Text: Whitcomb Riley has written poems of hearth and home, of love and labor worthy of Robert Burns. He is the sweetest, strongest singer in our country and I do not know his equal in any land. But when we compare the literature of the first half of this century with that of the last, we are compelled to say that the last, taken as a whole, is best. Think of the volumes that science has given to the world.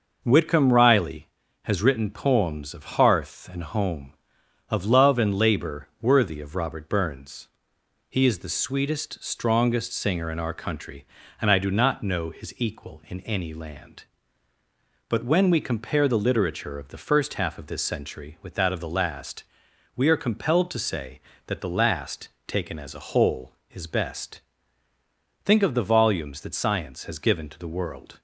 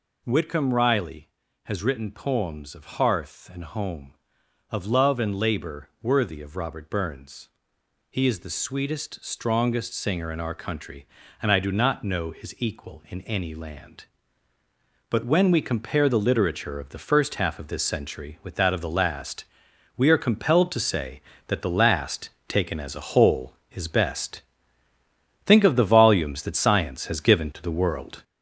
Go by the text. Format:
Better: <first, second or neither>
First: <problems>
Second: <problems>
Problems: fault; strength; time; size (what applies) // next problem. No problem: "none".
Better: first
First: none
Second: gets louder; noticeable; throughout; 5.5 dB